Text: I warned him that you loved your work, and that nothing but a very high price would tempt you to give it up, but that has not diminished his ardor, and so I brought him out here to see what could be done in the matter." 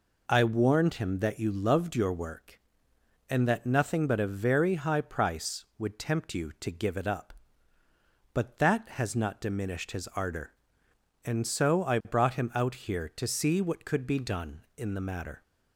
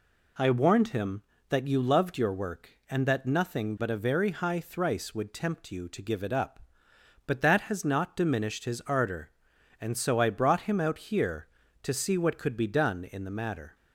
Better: first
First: none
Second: says "thrice" for "price"; at 4.6 s

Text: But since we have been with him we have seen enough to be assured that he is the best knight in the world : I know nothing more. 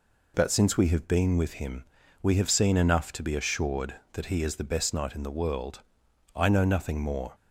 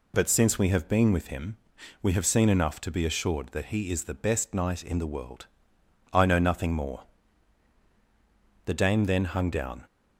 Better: first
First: pauses between "him" and "we"; at 1.8 s; 0.38 s long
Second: pauses between "him" and "we"; at 1.5 s; 0.44 s long // goes on to say "The dame then hung down"; noticeable; from 8.6 s on; 1.1 s long

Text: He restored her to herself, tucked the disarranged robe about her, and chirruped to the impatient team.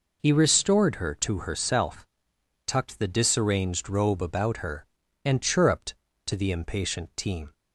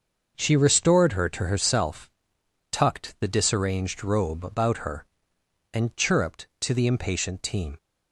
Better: first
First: none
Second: starts louder than the rest; noticeable; until 1.3 s; 6 dB // says "She" for "He"; at 0.3 s

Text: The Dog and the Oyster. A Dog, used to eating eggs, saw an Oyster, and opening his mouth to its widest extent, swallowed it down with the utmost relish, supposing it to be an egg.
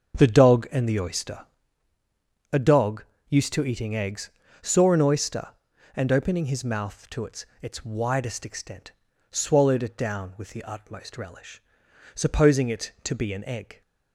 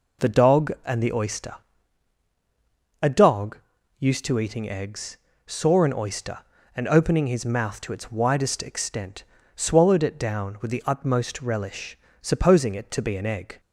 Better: second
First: starts louder than the rest; until 1.2 s; 7 dB // says "its" twice; at 7.5 s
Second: none

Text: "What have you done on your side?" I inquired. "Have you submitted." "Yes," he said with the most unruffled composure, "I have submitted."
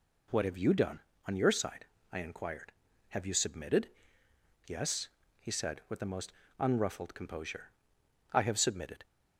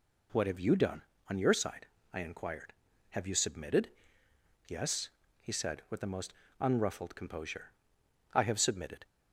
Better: neither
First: pauses between "most" and "unruffled"; slight; at 6.3 s; 0.26 s long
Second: pauses between "most" and "unruffled"; slight; at 6.3 s; 0.26 s long

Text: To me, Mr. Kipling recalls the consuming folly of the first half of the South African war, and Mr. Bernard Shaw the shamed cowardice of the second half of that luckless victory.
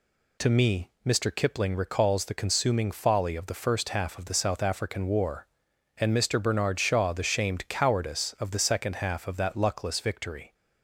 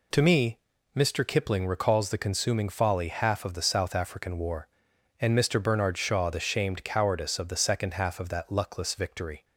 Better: first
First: none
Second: skips "of the first"; at 3.0 s

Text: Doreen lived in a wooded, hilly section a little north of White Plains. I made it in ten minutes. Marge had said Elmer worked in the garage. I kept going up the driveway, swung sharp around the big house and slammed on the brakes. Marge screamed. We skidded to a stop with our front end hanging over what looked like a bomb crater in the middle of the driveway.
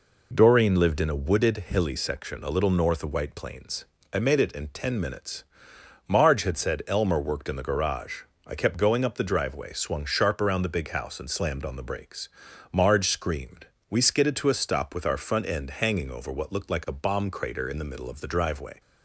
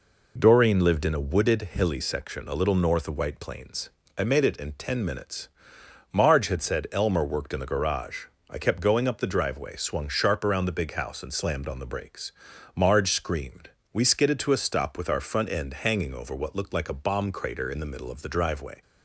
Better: neither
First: none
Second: none

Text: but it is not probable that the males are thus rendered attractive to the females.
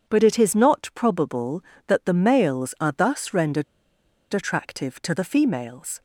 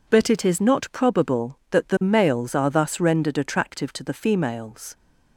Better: second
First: pauses between "rendered" and "attractive"; noticeable; at 3.6 s; 0.69 s long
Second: none

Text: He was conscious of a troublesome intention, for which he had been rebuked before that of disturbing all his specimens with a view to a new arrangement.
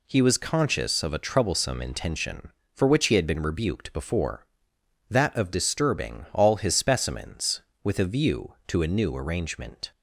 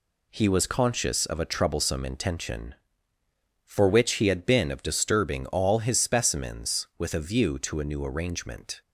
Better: first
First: none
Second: skips "rebuked before that"; at 4.6 s

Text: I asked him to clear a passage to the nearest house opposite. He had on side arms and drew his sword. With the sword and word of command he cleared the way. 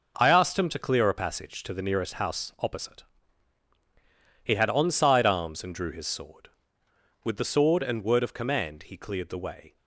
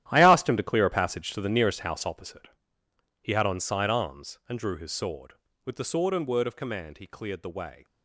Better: first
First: none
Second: gets quieter; strong; throughout; 13 dB

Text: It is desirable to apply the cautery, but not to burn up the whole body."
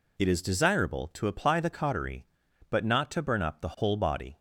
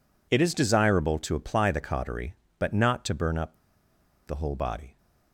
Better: first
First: none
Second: pauses between "up" and "the"; noticeable; at 3.5 s; 0.71 s long

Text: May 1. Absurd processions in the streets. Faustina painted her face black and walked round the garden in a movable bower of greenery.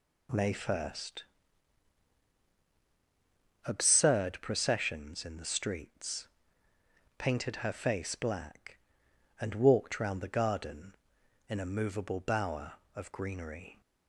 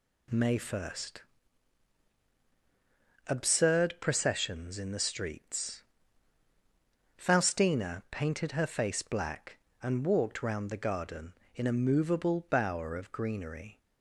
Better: second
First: skips "Faustina"; at 6.7 s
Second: none

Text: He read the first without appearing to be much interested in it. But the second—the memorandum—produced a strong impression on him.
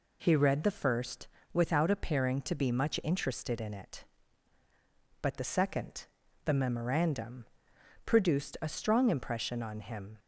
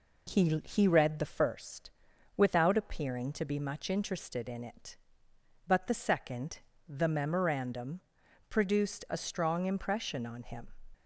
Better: first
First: pauses between "first" and "without"; slight; at 1.2 s; 0.25 s long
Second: says "He" twice; at 0.6 s // pauses between "first" and "without"; noticeable; at 1.9 s; 0.46 s long

